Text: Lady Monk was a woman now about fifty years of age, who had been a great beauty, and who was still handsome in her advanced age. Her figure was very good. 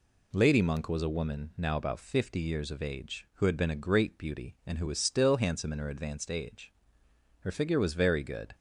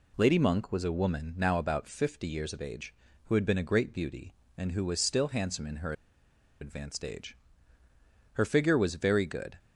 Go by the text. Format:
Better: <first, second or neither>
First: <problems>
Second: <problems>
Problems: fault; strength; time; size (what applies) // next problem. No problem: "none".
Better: first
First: none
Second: pauses between "her" and "advanced"; noticeable; at 5.9 s; 0.68 s long